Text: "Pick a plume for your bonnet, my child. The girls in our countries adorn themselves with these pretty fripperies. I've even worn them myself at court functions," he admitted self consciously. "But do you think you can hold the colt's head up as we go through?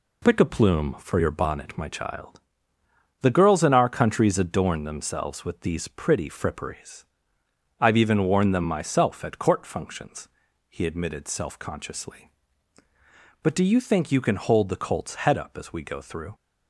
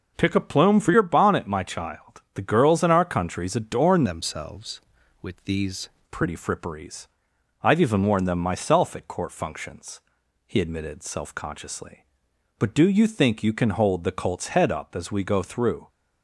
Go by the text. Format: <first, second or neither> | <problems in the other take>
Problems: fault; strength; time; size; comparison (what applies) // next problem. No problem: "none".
first | changes voice from "themselves" to "these"; from 4.0 to 5.8 s; 1.8 s long